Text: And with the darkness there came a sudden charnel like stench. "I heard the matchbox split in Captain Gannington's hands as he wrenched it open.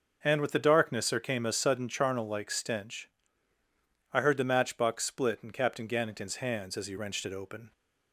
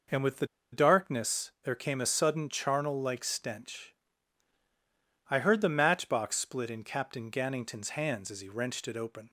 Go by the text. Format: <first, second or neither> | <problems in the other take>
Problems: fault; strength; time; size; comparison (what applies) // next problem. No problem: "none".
first | pauses between "the" and "darkness"; slight; at 0.4 s; 0.25 s long